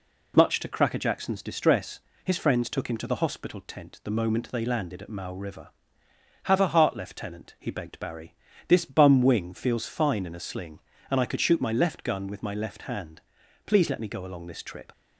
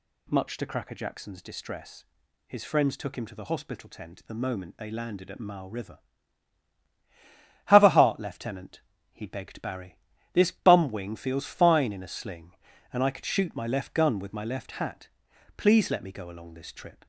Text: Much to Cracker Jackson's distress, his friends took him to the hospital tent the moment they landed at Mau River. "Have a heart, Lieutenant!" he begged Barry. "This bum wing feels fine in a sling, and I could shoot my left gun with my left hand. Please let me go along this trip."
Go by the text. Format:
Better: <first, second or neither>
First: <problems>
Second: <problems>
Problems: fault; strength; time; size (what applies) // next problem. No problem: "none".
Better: first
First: none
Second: says "hat" for "hand"; at 14.7 s